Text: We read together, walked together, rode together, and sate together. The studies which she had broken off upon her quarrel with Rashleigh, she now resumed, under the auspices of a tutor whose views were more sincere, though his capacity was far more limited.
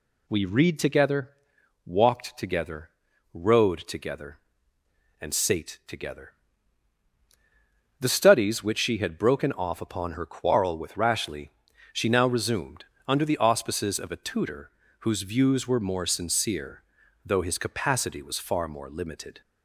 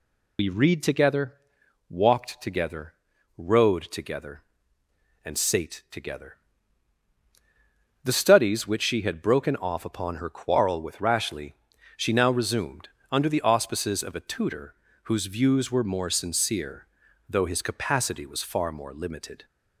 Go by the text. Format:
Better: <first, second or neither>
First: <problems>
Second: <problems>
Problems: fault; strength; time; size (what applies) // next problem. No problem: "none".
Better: first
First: pauses between "tutor" and "whose"; slight; at 14.7 s; 0.30 s long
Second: loses the start of "We"; at 0.3 s; 65 ms // pauses between "tutor" and "whose"; slight; at 14.7 s; 0.30 s long